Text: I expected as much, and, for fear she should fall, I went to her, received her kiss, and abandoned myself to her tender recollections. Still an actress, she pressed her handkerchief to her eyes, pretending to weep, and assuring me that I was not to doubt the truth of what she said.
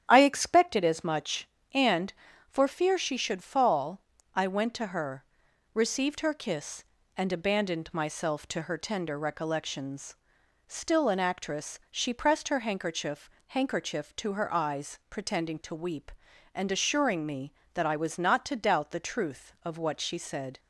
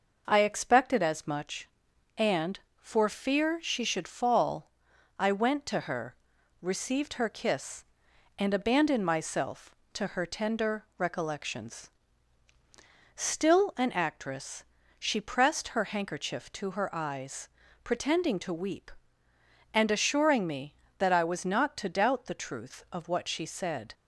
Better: second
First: starts louder than the rest; strong; until 1.0 s; 9.5 dB // says "handkerchief" twice; at 13.4 s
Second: none

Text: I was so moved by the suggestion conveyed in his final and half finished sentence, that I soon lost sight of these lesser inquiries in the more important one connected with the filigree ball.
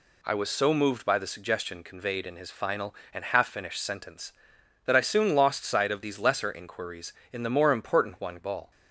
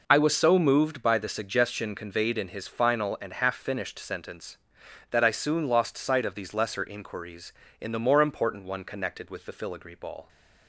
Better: second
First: skips "connected with the filigree"; at 8.4 s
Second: none

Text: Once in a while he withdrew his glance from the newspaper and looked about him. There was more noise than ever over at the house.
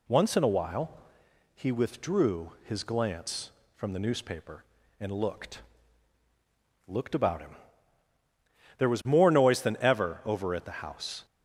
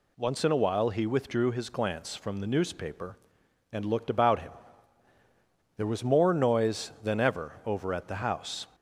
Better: second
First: pauses between "while" and "he"; noticeable; at 0.9 s; 0.64 s long // says "looked" twice; at 6.8 s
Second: none

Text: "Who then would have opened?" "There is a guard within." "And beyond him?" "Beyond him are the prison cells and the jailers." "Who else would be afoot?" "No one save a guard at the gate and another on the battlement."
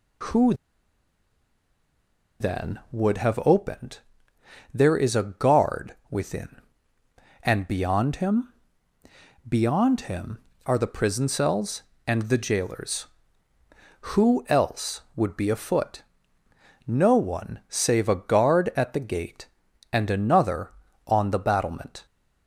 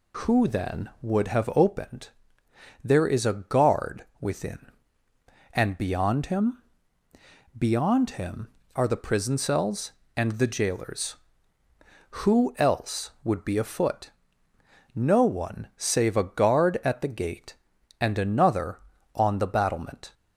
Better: second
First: pauses between "Who" and "then"; strong; at 0.5 s; 1.8 s long // pauses between "guard" and "within"; slight; at 5.9 s; 0.16 s long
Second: pauses between "guard" and "within"; slight; at 4.0 s; 0.16 s long

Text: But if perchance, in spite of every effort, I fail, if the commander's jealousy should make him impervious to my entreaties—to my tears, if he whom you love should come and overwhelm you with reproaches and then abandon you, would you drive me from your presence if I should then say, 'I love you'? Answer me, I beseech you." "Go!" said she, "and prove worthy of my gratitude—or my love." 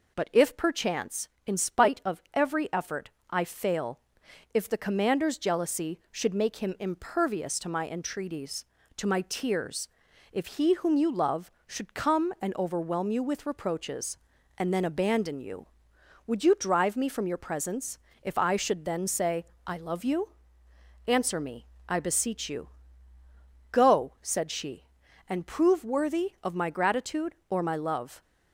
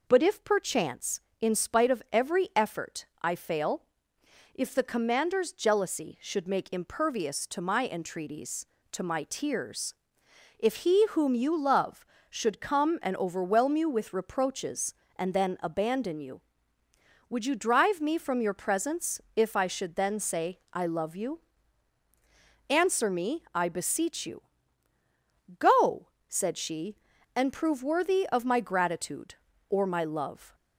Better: first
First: pauses between "presence" and "if"; slight; at 17.9 s; 0.24 s long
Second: skips "him"; at 6.7 s // pauses between "presence" and "if"; slight; at 19.1 s; 0.16 s long

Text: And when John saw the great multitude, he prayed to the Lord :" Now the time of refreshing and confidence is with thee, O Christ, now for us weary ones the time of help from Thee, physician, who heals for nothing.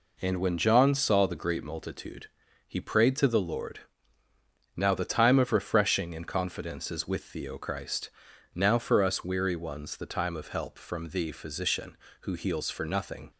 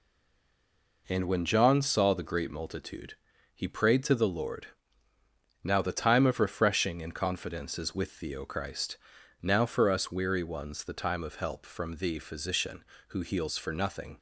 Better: first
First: none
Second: stays silent before the first word; until 1.0 s; 1.0 s long

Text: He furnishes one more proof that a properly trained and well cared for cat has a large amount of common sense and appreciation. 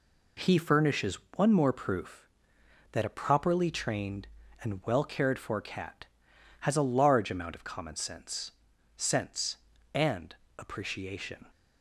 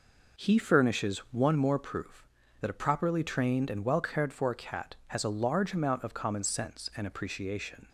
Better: second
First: pauses between "furnishes" and "one"; slight; at 1.1 s; 0.16 s long // says "sense" twice; at 8.9 s // pauses between "and" and "appreciation"; slight; at 10.3 s; 0.20 s long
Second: none

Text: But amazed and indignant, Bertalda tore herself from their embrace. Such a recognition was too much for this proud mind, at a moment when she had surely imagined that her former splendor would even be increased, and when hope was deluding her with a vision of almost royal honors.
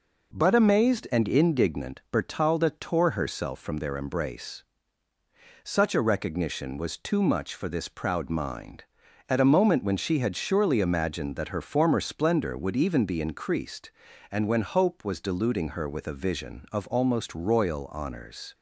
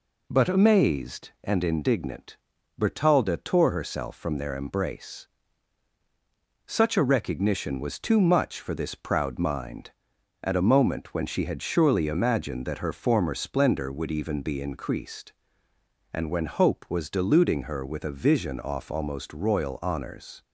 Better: first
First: none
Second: says "off" for "of"; at 18.5 s

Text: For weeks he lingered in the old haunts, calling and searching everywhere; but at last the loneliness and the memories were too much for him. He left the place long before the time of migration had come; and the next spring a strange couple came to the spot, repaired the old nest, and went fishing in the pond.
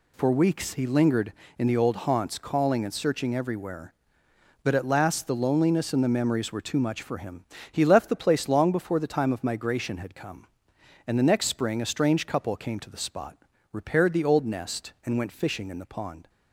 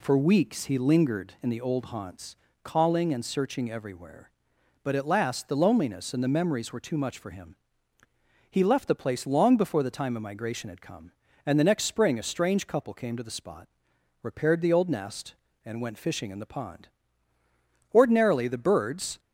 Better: first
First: none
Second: goes on to say "Ordinarily the birds"; noticeable; from 17.9 s on; 1.2 s long

